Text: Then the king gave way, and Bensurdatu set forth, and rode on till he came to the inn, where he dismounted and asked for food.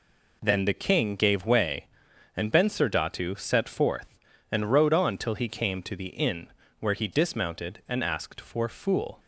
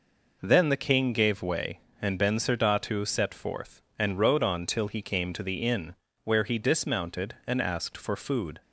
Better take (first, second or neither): second